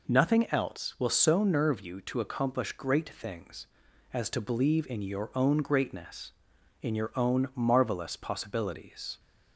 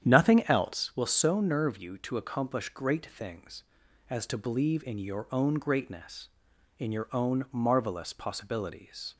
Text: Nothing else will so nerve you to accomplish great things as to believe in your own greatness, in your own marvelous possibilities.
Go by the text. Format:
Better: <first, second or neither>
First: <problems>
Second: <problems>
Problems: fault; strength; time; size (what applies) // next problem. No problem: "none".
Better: first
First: none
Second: starts louder than the rest; strong; until 1.0 s; 9.5 dB